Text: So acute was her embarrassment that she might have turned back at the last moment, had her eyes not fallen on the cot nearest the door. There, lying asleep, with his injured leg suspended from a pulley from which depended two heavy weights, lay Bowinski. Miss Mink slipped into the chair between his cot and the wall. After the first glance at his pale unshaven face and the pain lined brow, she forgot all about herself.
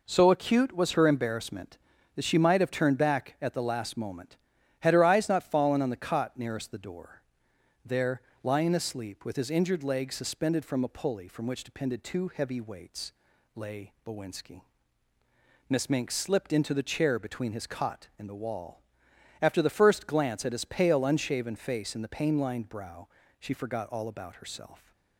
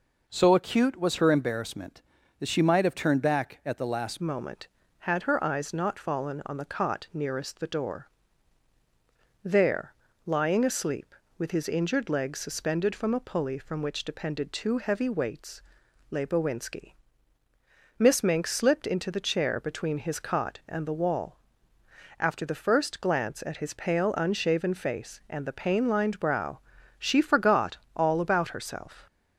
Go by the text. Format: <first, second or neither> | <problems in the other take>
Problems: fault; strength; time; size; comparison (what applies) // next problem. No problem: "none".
first | changes voice at "moment"; from 4.2 s on; 24.8 s long // pauses between "forgot" and "all"; slight; at 27.7 s; 0.18 s long